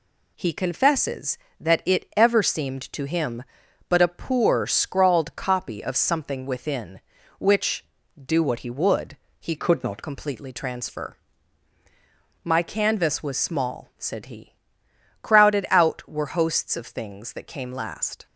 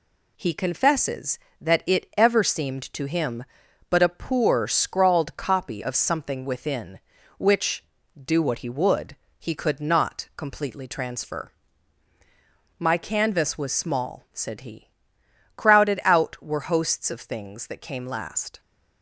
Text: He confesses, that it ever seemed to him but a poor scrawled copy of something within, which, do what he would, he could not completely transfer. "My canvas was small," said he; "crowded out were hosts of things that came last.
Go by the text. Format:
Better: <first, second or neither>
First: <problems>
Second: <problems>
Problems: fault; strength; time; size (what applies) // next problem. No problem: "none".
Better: second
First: changes voice from "could" to "not"; from 9.5 to 10.0 s; 0.5 s long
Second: none